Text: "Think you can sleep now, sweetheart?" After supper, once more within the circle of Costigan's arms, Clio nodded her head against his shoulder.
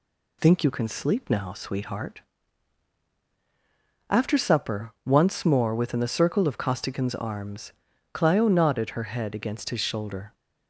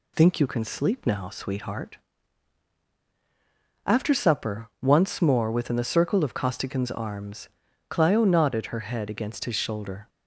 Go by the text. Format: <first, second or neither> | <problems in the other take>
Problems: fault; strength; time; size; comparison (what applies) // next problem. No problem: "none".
neither | none